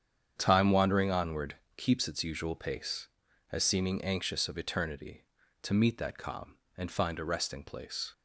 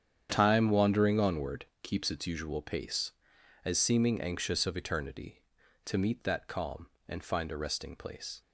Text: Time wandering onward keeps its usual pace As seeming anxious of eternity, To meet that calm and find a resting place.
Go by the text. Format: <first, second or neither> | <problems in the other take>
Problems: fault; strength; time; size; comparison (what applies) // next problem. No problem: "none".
neither | starts louder than the rest; strong; the same in both // pauses between "onward" and "keeps"; slight; the same in both